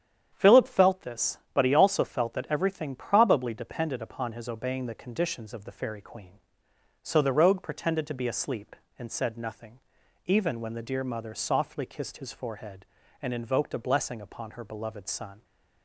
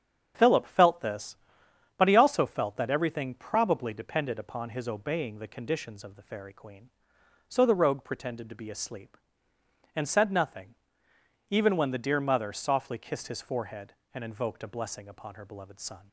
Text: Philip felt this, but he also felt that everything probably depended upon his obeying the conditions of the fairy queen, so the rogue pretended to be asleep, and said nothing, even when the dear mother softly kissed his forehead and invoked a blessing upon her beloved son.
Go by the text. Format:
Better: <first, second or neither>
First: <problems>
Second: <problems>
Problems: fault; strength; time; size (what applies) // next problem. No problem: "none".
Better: neither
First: starts louder than the rest; strong; until 1.3 s; 9 dB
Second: starts louder than the rest; strong; until 1.3 s; 8 dB